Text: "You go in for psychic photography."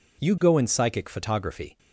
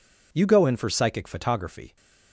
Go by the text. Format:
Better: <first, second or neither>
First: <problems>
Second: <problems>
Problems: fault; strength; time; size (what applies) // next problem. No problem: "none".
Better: second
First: skips "for"; at 0.6 s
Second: none